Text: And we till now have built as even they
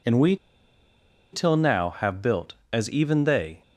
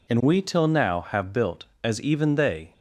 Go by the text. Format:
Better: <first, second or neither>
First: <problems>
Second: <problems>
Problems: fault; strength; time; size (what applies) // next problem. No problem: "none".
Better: second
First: pauses between "we" and "till"; noticeable; at 0.3 s; 0.97 s long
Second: none